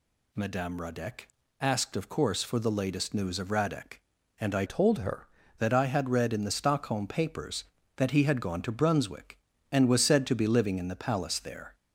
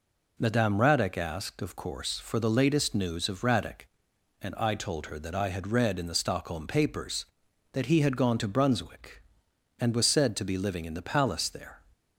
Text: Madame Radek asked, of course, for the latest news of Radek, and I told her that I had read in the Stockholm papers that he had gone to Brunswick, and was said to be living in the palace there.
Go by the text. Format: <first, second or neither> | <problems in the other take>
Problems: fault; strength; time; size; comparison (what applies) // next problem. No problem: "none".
second | pauses between "Radek" and "asked"; slight; at 1.2 s; 0.32 s long // changes voice from "told" to "her"; from 4.6 to 5.2 s; 0.6 s long